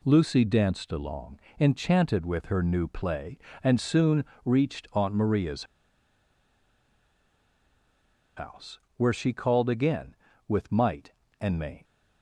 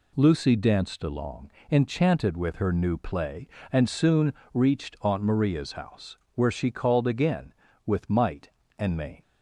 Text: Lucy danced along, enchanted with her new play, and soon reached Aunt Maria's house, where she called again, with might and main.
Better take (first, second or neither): second